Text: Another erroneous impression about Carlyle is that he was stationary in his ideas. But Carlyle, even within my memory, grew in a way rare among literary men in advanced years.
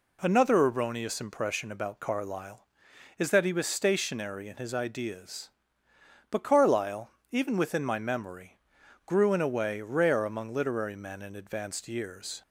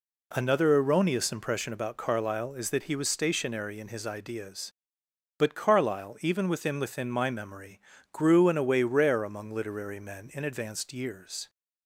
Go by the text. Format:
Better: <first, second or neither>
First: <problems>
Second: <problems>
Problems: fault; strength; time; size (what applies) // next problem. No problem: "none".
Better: first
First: none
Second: says "within" twice; at 6.7 s